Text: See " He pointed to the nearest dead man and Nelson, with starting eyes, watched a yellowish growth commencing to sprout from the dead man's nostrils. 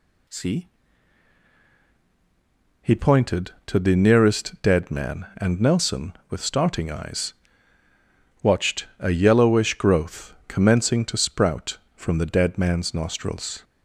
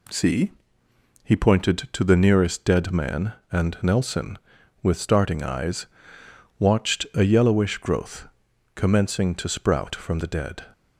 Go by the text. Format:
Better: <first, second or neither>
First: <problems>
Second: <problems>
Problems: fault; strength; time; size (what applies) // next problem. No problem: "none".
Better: first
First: none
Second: pauses between "growth" and "commencing"; noticeable; at 8.2 s; 0.46 s long // stops before "man's nostrils"; at 10.7 s